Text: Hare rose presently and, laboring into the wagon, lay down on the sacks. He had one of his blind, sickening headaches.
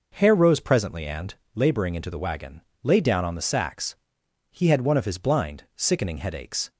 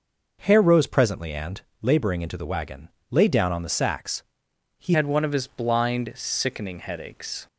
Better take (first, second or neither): first